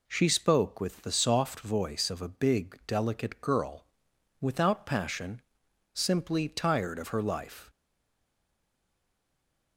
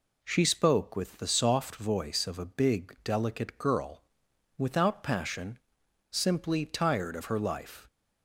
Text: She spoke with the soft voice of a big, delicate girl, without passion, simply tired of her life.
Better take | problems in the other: second | stays silent after the last word; noticeable; from 7.6 s on; 2.1 s long

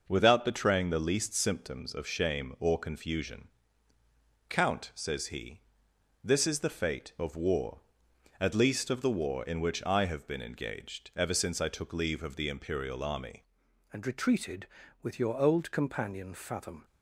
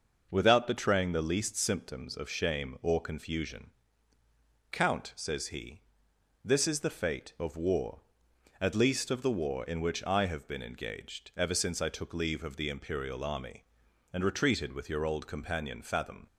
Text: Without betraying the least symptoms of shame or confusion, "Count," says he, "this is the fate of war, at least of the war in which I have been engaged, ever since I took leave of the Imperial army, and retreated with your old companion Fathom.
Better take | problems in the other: second | changes voice at "and"; from 13.9 s on; 2.9 s long

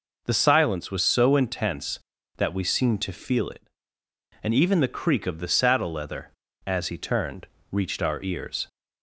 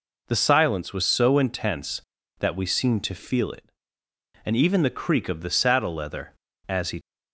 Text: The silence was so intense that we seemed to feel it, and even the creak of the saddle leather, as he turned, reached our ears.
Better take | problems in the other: first | stops before "turned reached our ears"; at 7.0 s

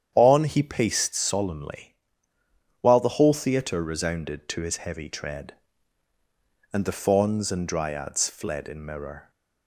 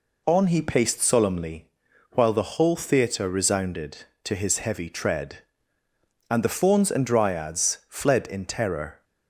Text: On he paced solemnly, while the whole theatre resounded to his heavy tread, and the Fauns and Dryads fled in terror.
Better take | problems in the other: second | starts louder than the rest; strong; until 1.1 s; 9 dB // says "mirror" for "terror"; at 8.8 s

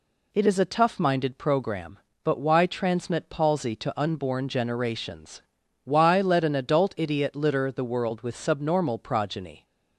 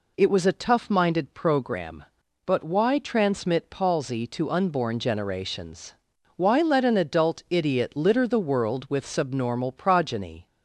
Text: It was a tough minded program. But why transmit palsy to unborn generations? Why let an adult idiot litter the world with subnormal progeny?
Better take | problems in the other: second | says "is" for "was"; at 0.4 s

